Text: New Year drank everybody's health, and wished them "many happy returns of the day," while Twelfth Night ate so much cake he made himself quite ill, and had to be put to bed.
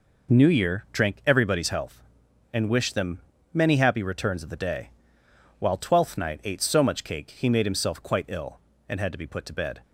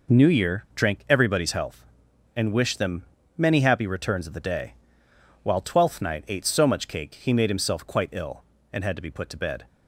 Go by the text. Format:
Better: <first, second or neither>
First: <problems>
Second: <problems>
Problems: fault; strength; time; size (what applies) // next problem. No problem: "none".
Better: neither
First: pauses between "them" and "many"; slight; at 3.1 s; 0.36 s long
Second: pauses between "them" and "many"; slight; at 3.0 s; 0.36 s long